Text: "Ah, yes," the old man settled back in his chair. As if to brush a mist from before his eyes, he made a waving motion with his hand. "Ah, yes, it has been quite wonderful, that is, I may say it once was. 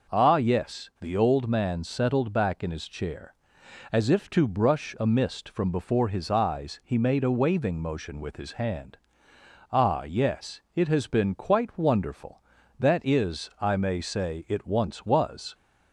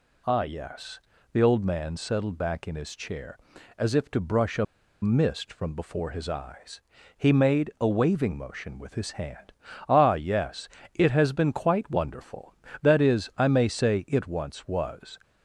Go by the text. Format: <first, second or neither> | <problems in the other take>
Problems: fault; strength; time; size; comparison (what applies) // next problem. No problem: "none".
first | pauses between "a" and "mist"; at 4.6 s; 0.37 s long